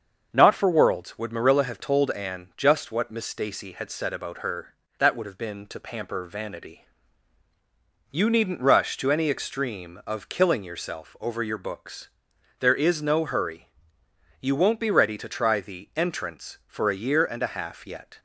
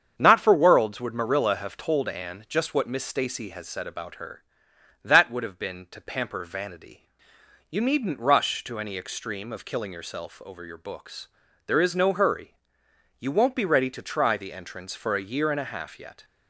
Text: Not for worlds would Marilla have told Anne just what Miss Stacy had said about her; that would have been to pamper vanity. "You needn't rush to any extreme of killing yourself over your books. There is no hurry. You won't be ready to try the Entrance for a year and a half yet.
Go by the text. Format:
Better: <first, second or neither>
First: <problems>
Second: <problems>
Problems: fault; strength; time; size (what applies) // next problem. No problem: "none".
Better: first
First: starts louder than the rest; until 1.3 s; 6.5 dB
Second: starts louder than the rest; strong; until 1.1 s; 7.5 dB // says "has" for "had"; at 3.5 s